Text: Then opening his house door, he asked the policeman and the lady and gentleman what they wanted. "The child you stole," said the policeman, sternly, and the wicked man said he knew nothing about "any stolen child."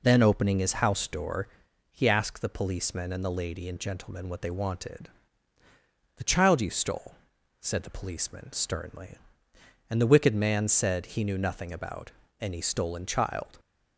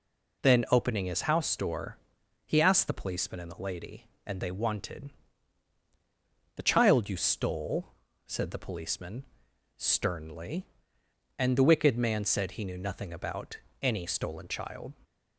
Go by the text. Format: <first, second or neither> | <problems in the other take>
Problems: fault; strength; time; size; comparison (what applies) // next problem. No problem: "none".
first | skips "gentleman what"; at 4.4 s // pauses between "about" and "any"; slight; at 13.5 s; 0.24 s long; slight in the first